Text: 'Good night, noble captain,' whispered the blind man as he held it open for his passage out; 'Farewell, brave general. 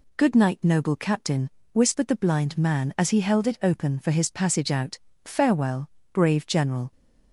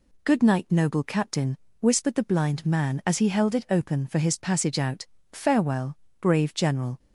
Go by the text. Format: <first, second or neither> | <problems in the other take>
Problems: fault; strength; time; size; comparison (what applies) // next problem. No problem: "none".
neither | none